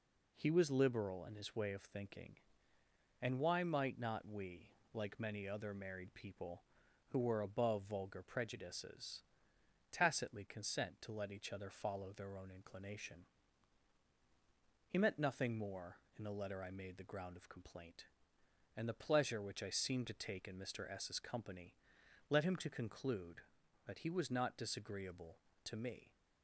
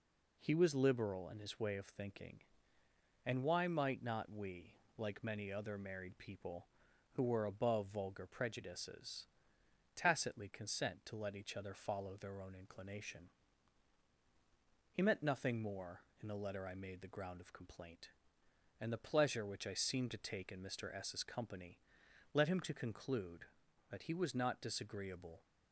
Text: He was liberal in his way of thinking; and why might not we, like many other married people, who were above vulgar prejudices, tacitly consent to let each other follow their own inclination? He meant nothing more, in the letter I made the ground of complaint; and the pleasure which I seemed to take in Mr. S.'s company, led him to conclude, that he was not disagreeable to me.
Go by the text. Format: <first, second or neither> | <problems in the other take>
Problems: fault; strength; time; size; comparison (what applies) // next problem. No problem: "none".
first | stops before "to me"; at 25.4 s